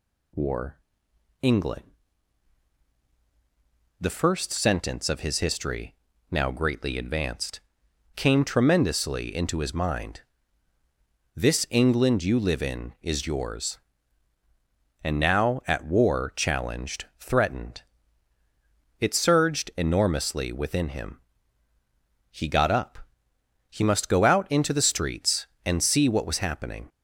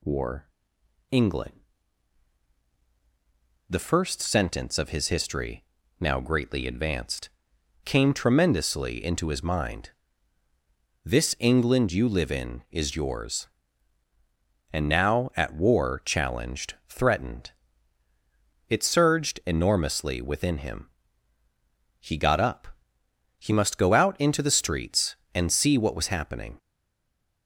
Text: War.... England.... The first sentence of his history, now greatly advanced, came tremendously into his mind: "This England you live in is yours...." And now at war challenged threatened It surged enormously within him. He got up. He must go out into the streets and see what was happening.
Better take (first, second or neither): first